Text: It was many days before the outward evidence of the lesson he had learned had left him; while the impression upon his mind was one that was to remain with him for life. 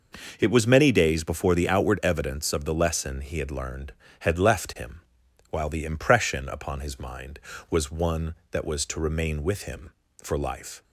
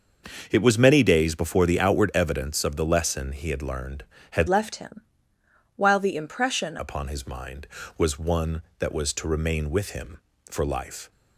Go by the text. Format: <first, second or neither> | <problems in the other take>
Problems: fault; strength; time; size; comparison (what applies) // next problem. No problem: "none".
first | starts louder than the rest; noticeable; until 1.5 s; 6 dB // changes voice from "left" to "impression"; from 4.4 to 6.7 s; 2.3 s long